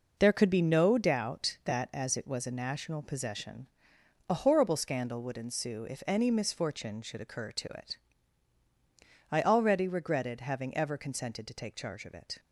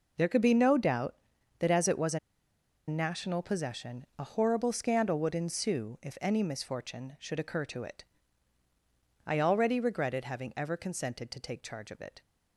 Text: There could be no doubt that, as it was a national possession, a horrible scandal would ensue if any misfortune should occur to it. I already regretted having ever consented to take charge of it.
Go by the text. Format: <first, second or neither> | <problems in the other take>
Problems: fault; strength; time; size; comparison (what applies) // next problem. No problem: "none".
first | pauses between "a" and "national"; noticeable; at 2.1 s; 0.69 s long